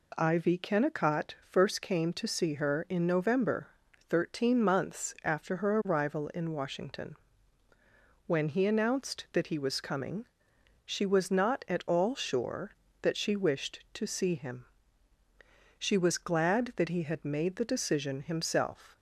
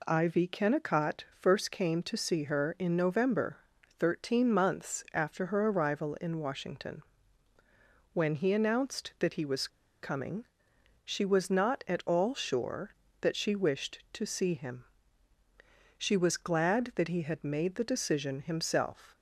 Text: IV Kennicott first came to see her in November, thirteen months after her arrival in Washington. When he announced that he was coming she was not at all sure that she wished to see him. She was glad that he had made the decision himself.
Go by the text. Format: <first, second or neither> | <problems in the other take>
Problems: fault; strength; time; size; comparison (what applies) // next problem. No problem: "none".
first | pauses between "Kennicott" and "first"; slight; at 1.2 s; 0.16 s long; slight in the first // pauses between "was" and "coming"; slight; at 9.6 s; 0.34 s long // pauses between "coming" and "she"; noticeable; at 10.4 s; 0.60 s long; noticeable in the first